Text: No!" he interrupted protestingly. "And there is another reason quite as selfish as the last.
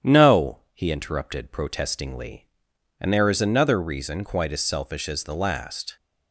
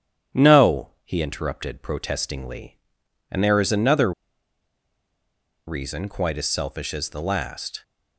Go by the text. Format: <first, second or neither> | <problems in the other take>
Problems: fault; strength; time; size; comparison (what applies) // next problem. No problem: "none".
first | starts louder than the rest; strong; until 1.4 s; 9.5 dB; strong in the first // pauses between "another" and "reason"; strong; at 4.1 s; 1.5 s long